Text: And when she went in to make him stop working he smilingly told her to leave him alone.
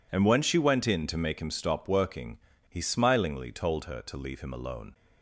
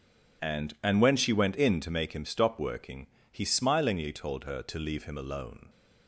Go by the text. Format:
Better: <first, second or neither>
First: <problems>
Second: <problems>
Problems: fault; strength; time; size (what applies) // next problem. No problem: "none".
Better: first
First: pauses between "working" and "he"; slight; at 2.3 s; 0.30 s long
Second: says "And" twice; at 0.8 s // pauses between "working" and "he"; slight; at 3.0 s; 0.24 s long